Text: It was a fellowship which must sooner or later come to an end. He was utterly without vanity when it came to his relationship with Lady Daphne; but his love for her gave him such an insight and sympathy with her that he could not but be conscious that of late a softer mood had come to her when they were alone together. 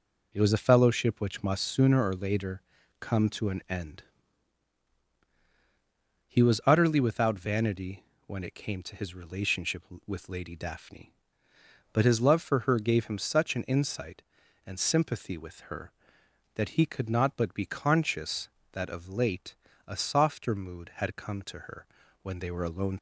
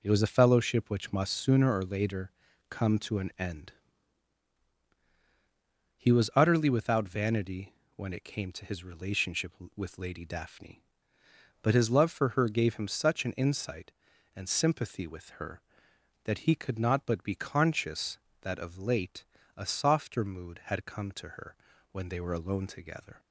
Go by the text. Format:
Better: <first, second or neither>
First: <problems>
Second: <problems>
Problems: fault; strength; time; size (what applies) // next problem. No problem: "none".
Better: second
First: pauses between "later" and "come"; at 2.6 s; 0.38 s long // pauses between "vanity" and "when"; slight; at 8.0 s; 0.22 s long // pauses between "late" and "a"; slight; at 19.5 s; 0.30 s long // pauses between "her" and "when"; slight; at 21.8 s; 0.36 s long // stops before "together"; at 22.9 s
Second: pauses between "later" and "come"; at 2.3 s; 0.38 s long // pauses between "vanity" and "when"; slight; at 7.7 s; 0.22 s long // pauses between "late" and "a"; slight; at 19.2 s; 0.30 s long // pauses between "her" and "when"; slight; at 21.5 s; 0.36 s long